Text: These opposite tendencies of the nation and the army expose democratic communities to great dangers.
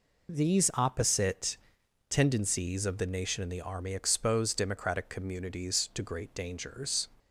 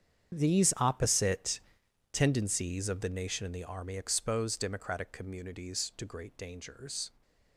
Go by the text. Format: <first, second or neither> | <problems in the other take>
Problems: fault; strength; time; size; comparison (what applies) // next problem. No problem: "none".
first | gets quieter; strong; throughout; 15 dB // pauses between "opposite" and "tendencies"; noticeable; at 1.5 s; 0.52 s long; noticeable in the first